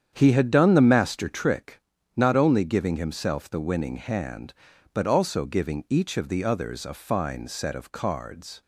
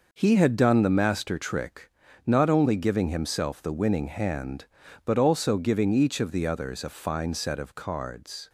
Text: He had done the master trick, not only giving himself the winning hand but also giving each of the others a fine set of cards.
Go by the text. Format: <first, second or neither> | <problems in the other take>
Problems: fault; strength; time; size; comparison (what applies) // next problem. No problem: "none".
second | starts louder than the rest; strong; until 1.5 s; 8.5 dB